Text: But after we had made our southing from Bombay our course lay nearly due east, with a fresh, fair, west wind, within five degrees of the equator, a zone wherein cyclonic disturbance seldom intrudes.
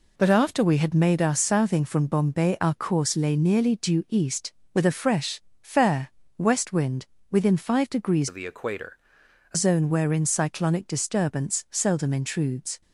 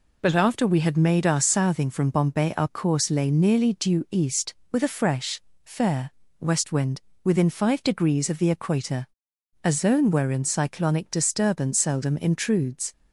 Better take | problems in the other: second | changes voice from "of" to "a"; from 8.2 to 9.5 s; 1.3 s long

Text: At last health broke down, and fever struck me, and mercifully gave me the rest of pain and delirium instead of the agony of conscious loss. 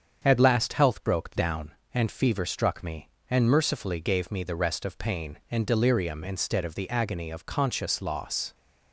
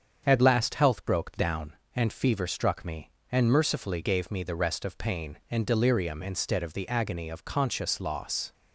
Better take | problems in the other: neither | starts louder than the rest; strong; the same in both

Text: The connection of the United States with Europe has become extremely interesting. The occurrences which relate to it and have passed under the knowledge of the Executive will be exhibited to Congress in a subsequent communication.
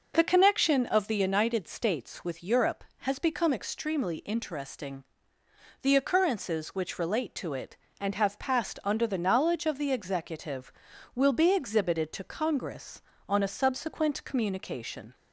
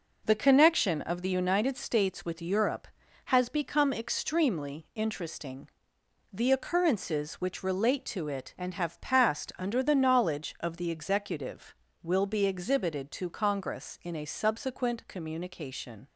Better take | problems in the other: second | says "on" for "in"; at 13.2 s

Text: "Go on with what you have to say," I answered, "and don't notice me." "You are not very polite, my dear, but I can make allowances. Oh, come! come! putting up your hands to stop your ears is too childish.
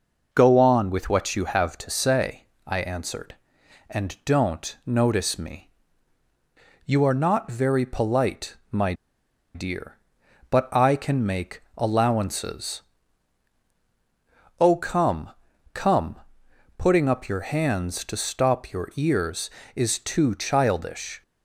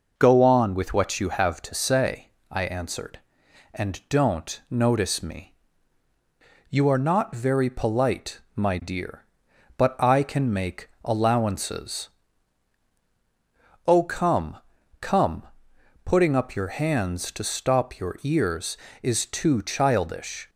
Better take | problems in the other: second | pauses between "my" and "dear"; noticeable; at 8.9 s; 0.61 s long

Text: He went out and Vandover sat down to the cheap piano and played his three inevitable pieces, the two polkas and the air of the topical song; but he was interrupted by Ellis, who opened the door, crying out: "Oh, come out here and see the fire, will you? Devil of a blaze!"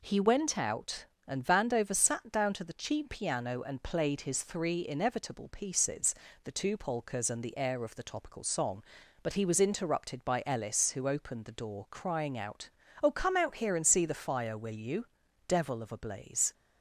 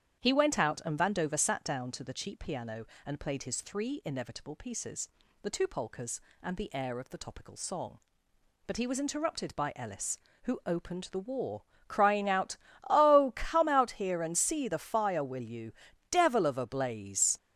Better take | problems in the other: first | starts louder than the rest; strong; until 1.2 s; 9 dB // says "war" for "door"; at 11.1 s

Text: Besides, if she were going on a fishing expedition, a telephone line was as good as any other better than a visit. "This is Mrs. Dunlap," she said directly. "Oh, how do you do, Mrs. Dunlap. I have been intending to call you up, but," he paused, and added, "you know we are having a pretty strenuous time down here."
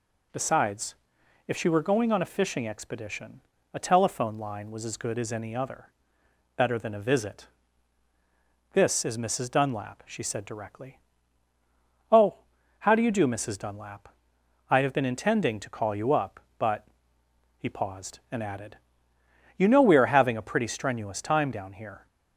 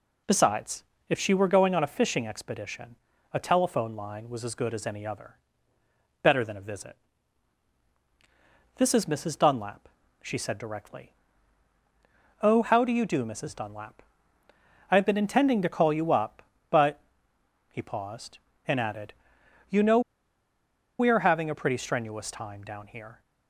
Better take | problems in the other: first | pauses between "other" and "better"; noticeable; at 5.3 s; 0.86 s long; noticeable in the first // pauses between "know" and "we"; at 19.9 s; 0.99 s long

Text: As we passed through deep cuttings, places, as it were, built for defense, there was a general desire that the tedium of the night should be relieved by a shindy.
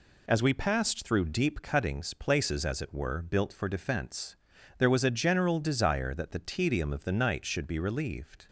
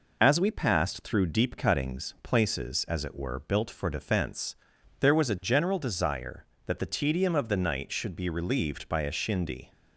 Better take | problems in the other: second | stops before "by a shindy"; at 8.4 s

